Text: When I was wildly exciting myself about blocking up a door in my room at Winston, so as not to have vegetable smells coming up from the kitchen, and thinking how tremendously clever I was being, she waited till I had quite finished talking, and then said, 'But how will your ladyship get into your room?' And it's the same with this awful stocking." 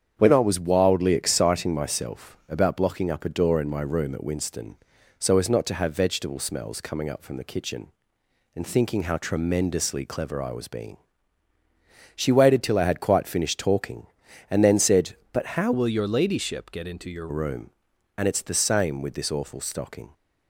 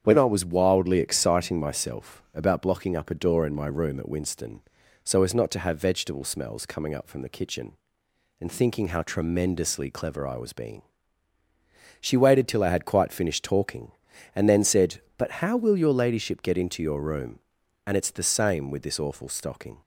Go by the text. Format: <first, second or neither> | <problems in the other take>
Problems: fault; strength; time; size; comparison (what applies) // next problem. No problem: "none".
second | starts louder than the rest; strong; until 1.1 s; 8 dB; strong in the second // changes voice from "will" to "your"; from 15.7 to 17.2 s; 1.5 s long